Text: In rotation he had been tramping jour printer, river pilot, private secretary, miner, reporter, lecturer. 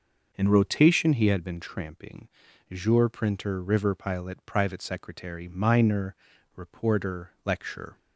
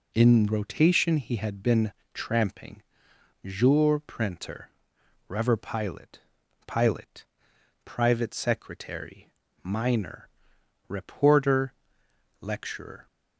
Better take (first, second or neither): first